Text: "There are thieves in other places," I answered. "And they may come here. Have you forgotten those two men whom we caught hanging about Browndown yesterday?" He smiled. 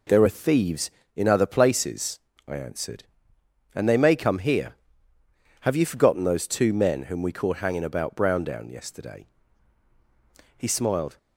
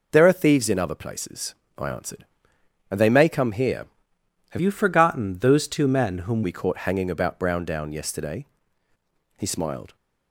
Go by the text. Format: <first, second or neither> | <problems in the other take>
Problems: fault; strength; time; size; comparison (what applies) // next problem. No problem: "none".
first | changes voice from "you" to "whom"; from 4.5 to 6.4 s; 1.9 s long